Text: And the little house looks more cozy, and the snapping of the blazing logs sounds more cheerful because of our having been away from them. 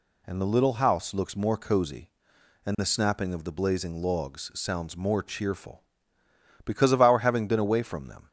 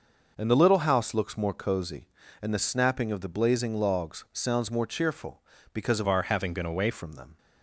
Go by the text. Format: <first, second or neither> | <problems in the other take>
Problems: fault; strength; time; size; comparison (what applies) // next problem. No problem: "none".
first | changes voice from "our" to "away"; from 6.0 to 6.9 s; 0.9 s long